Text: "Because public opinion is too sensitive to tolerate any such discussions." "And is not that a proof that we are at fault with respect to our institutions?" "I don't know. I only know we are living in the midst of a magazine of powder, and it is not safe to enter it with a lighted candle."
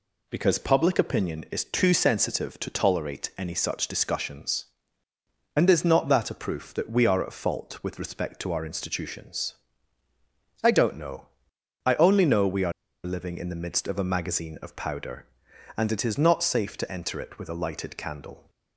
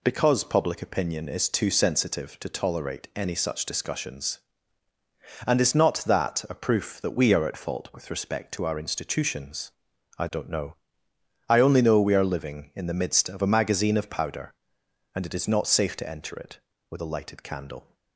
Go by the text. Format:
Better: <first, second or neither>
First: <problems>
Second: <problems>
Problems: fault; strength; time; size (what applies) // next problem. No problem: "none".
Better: second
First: pauses between "are" and "living"; slight; at 12.7 s; 0.33 s long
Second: none